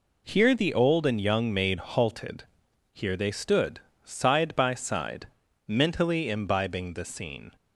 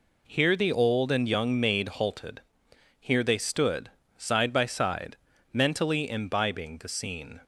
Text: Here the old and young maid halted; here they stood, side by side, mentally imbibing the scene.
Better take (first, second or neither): neither